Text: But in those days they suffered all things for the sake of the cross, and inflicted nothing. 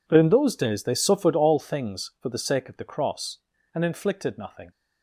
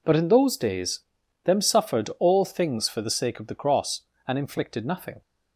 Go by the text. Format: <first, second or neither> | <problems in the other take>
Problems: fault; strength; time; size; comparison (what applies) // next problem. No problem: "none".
first | says "them" for "they"; at 1.4 s